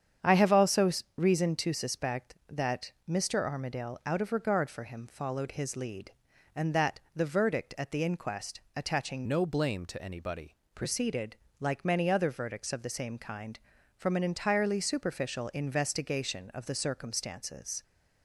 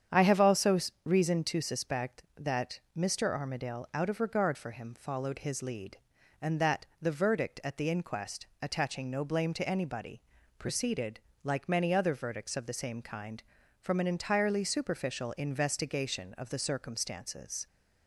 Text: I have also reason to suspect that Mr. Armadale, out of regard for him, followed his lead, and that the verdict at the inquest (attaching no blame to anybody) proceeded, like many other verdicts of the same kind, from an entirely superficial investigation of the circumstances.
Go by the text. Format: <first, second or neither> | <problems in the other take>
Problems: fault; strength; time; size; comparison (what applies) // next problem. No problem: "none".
second | starts louder than the rest; strong; until 1.4 s; 8 dB; strong in the second // pauses between "also" and "reason"; slight; at 0.9 s; 0.26 s long; slight in the second // pauses between "that" and "the"; slight; at 7.0 s; 0.16 s long; slight in the second // changes voice from "no" to "anybody"; from 9.2 to 10.5 s; 1.3 s long